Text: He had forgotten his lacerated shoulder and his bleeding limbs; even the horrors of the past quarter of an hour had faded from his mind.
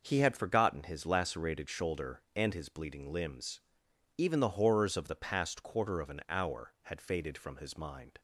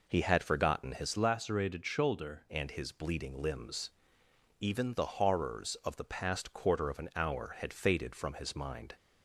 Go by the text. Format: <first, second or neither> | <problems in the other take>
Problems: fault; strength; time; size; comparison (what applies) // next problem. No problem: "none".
first | changes voice from "lacerated" to "shoulder"; from 1.1 to 2.4 s; 1.3 s long